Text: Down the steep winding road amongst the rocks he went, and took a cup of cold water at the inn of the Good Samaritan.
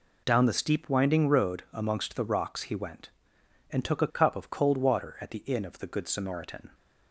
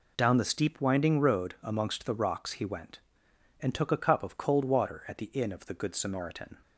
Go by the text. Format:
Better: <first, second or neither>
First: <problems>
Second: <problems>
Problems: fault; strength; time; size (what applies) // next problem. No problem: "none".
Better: neither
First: none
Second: none